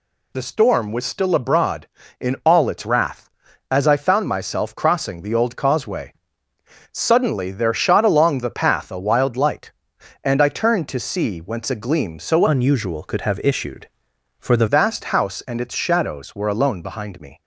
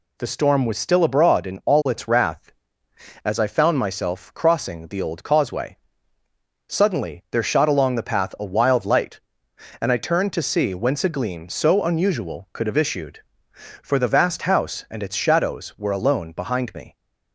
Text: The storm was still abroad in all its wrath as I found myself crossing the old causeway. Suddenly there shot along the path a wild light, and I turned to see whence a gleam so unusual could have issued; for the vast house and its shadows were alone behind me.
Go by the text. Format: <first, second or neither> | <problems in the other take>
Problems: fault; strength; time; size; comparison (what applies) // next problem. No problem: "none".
second | changes voice from "unusual" to "the"; from 12.4 to 14.6 s; 2.2 s long